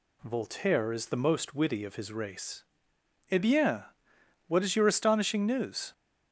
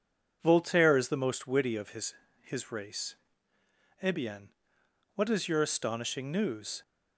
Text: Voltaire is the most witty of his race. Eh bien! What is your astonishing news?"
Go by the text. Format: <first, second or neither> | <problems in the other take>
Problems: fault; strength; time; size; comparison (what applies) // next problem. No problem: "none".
first | says "his" twice; at 2.4 s